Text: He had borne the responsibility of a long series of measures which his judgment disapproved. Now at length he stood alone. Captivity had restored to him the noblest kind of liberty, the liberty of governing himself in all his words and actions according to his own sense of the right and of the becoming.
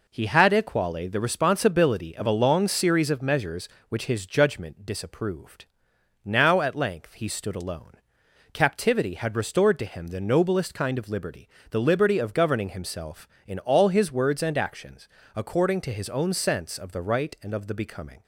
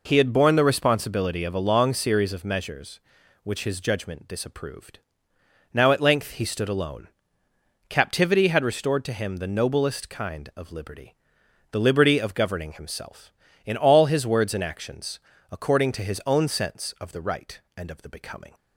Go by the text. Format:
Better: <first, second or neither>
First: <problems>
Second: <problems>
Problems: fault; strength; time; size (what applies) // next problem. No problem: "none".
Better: second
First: says "equale" for "borne"; at 0.5 s // pauses between "actions" and "according"; slight; at 15.0 s; 0.28 s long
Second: pauses between "actions" and "according"; slight; at 15.1 s; 0.32 s long